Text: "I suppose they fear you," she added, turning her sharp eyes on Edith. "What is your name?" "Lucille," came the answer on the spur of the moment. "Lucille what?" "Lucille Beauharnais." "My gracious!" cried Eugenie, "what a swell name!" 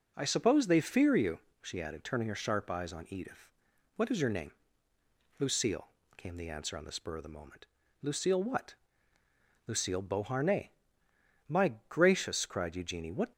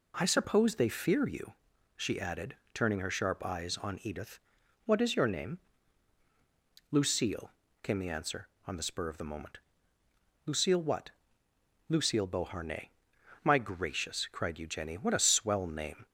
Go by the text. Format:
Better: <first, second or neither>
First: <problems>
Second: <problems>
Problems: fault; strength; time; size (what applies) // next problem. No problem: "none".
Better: second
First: stops before "a swell name"; at 13.3 s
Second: none